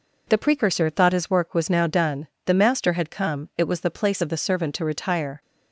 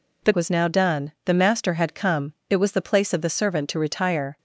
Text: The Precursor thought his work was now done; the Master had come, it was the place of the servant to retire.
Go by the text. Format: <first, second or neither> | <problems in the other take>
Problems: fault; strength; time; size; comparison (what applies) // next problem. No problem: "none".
first | skips "Precursor thought his work"; at 0.3 s